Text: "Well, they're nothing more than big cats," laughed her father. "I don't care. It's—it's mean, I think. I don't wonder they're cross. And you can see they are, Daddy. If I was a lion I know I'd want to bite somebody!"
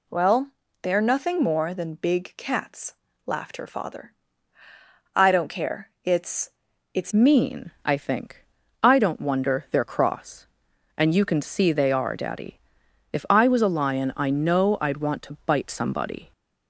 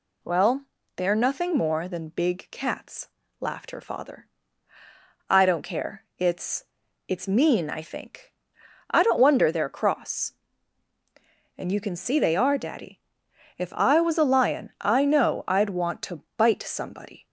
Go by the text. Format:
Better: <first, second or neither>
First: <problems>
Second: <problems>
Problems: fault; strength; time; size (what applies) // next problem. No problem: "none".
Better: second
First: changes voice at "mean"; from 7.1 s on; 9.2 s long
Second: none